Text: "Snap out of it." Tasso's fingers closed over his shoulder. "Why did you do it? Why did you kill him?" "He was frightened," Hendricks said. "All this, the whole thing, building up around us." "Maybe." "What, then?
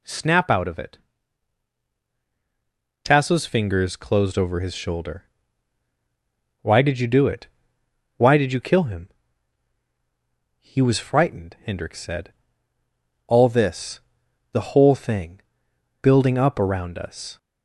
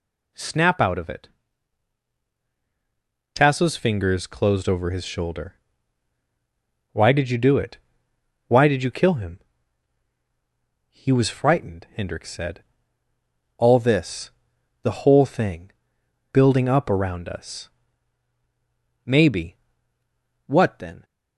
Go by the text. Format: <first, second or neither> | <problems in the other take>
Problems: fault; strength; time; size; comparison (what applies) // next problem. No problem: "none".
second | stops before "Maybe What then"; at 17.3 s